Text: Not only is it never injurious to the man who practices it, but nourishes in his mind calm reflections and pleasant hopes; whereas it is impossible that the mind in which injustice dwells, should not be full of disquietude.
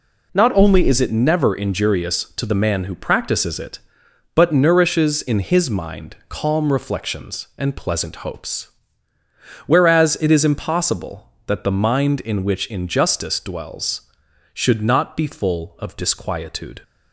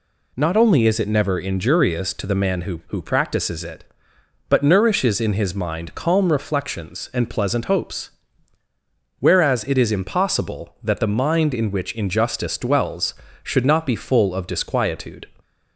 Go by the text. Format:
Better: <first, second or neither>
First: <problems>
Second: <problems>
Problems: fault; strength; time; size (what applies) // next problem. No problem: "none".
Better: first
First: none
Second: says "who" twice; at 2.8 s